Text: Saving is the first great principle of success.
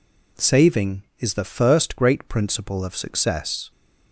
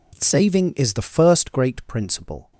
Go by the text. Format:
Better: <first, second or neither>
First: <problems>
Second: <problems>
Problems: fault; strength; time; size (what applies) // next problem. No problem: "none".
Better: first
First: none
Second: stops before "of success"; at 2.5 s